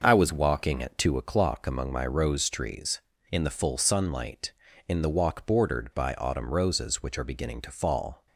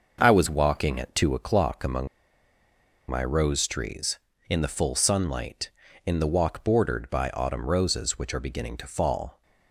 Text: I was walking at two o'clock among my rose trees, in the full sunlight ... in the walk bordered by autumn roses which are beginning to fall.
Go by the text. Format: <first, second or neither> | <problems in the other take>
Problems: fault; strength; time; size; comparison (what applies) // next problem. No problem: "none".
first | starts louder than the rest; noticeable; until 1.2 s; 6 dB; noticeable in the first // pauses between "among" and "my"; at 2.0 s; 1.0 s long